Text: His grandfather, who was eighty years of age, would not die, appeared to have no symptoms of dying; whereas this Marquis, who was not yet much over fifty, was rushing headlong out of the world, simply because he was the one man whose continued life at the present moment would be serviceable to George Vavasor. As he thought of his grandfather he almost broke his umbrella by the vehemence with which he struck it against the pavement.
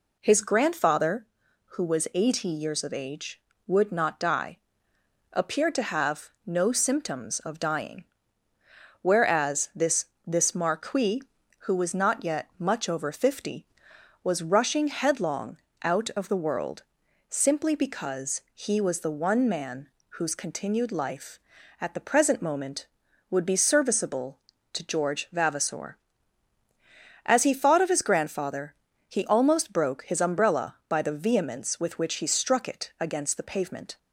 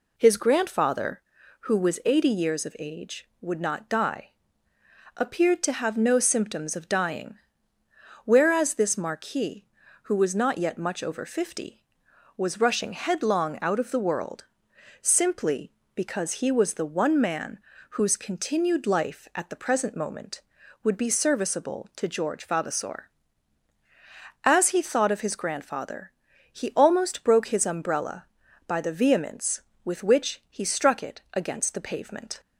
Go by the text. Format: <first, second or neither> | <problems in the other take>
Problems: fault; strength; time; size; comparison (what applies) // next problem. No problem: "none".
second | pauses between "have" and "no"; slight; at 6.2 s; 0.16 s long // says "this" twice; at 10.2 s // pauses between "headlong" and "out"; slight; at 15.5 s; 0.26 s long // pauses between "man" and "whose"; slight; at 19.8 s; 0.30 s long; slight in the second // pauses between "grandfather" and "he"; slight; at 28.7 s; 0.36 s long; also in the second